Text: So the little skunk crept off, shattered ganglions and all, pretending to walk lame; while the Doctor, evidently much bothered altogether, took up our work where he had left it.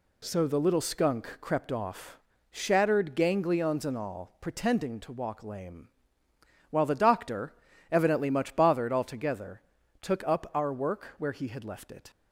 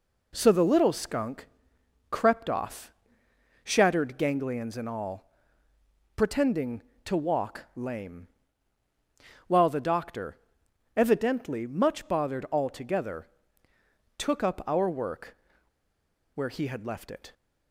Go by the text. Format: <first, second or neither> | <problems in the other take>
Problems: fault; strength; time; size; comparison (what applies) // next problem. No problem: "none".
first | pauses between "skunk" and "crept"; noticeable; at 1.4 s; 0.64 s long // pauses between "work" and "where"; noticeable; at 15.3 s; 0.97 s long